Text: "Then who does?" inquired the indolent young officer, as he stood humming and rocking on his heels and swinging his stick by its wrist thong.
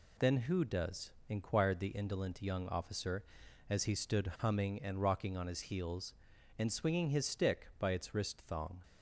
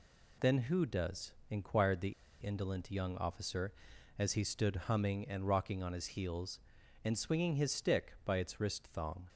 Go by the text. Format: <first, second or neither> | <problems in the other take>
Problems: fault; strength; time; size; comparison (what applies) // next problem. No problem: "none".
first | pauses between "the" and "indolent"; slight; at 2.1 s; 0.30 s long